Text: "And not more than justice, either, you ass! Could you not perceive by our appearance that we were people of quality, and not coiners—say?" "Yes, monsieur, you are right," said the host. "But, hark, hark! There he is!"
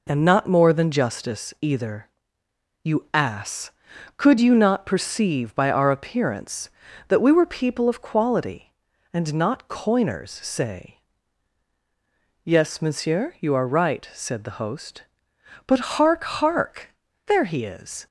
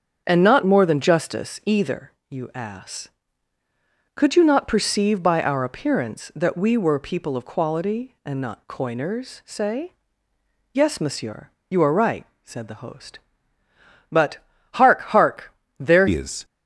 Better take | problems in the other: first | starts louder than the rest; strong; until 1.2 s; 8 dB // changes voice at "he"; from 16.0 s on; 0.4 s long

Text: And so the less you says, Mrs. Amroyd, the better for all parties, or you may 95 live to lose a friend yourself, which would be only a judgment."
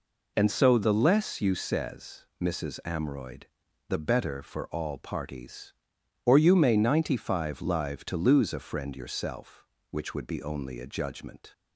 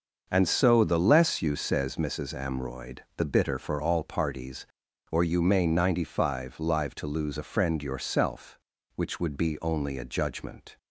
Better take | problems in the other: first | starts louder than the rest; until 1.3 s; 6 dB // says "bitter" for "better"; at 3.2 s

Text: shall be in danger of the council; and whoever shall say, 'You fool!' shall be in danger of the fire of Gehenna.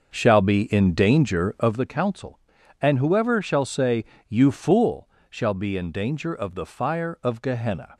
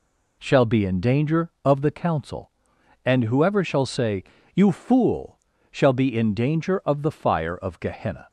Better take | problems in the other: second | starts louder than the rest; until 1.8 s; 6.5 dB

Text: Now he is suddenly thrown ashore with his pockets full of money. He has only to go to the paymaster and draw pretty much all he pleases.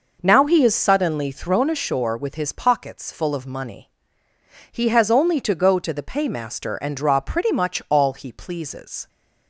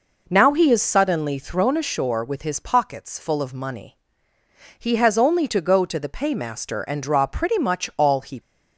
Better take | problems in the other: first | stops before "pleases"; at 8.3 s

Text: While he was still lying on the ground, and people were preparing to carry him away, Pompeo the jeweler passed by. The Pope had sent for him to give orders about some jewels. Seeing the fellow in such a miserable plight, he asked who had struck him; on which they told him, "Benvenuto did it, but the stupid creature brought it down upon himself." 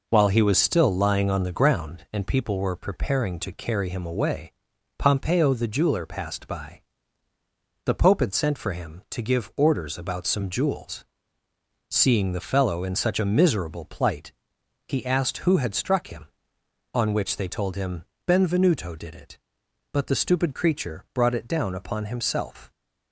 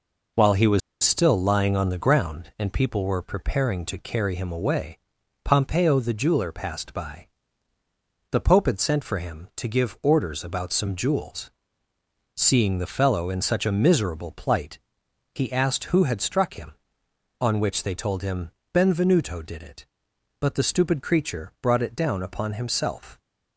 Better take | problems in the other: first | pauses between "was" and "still"; slight; at 0.8 s; 0.23 s long

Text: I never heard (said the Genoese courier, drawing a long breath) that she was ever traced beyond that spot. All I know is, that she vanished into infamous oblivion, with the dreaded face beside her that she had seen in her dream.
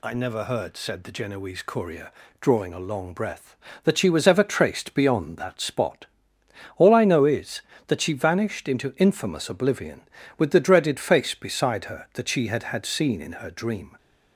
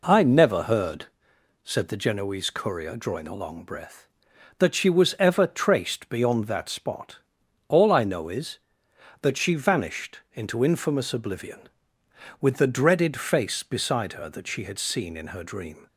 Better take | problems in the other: second | says "had" twice; at 12.6 s

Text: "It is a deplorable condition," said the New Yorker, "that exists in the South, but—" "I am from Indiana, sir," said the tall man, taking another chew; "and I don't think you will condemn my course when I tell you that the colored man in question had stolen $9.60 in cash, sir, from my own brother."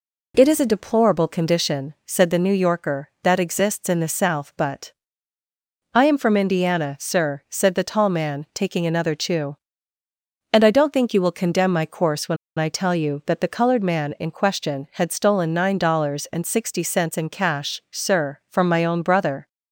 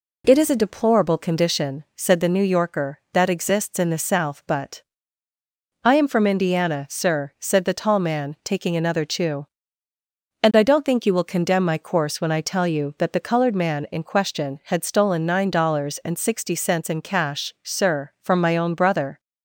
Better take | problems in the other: second | pauses between "when" and "I"; slight; at 12.3 s; 0.21 s long

